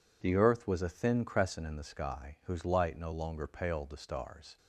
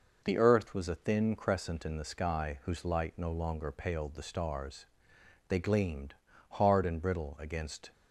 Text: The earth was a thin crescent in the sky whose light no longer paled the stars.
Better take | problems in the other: first | goes on to say "They gleamed hard and brittle against"; strong; from 5.4 s on; 2.4 s long

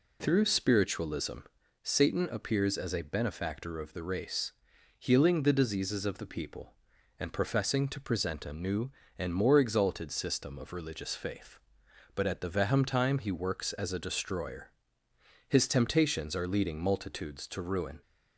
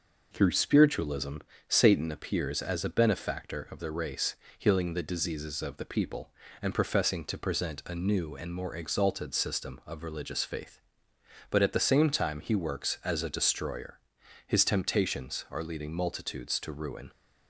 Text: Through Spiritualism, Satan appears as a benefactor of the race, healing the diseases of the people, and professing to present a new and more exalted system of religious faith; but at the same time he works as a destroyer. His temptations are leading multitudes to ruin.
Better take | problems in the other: second | says "vehem" for "same"; at 12.5 s

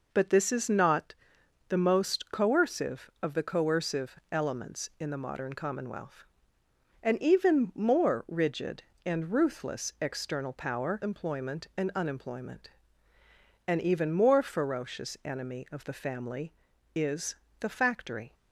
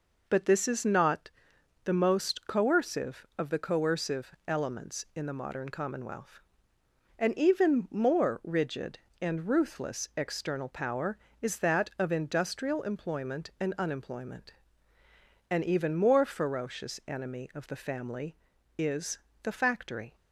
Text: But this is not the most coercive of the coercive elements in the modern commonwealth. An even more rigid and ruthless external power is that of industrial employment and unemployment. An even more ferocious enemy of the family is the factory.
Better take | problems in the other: second | pauses between "not" and "the"; noticeable; at 1.1 s; 0.54 s long; noticeable in the second // skips "is that of industrial"; at 11.0 s // pauses between "is" and "the"; slight; at 17.3 s; 0.24 s long; slight in the second

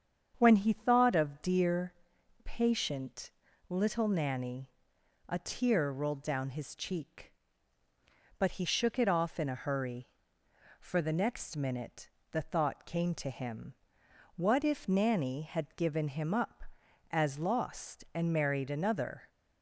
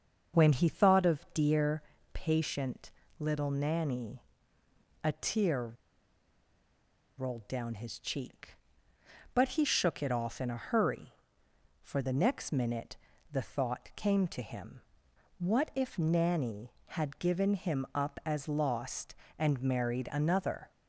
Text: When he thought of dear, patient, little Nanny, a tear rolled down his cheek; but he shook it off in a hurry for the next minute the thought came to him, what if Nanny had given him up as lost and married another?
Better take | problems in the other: first | starts louder than the rest; until 1.4 s; 6.5 dB; strong in the first // pauses between "tear" and "rolled"; strong; at 5.7 s; 1.4 s long // pauses between "minute" and "the"; slight; at 12.9 s; 0.34 s long; slight in the first

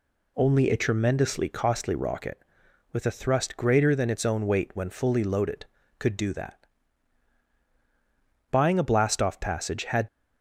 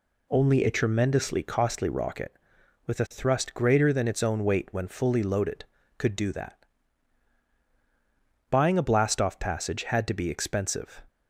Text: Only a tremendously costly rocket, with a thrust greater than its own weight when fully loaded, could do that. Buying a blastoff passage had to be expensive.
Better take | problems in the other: second | stops before "to be expensive"; at 10.0 s

